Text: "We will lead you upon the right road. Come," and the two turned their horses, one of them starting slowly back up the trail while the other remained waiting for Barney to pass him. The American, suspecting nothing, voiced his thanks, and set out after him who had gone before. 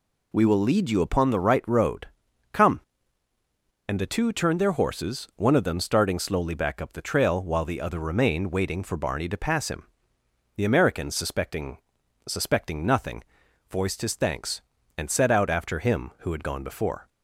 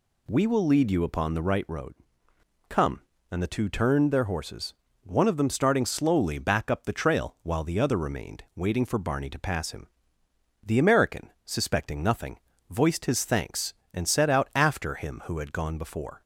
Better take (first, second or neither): second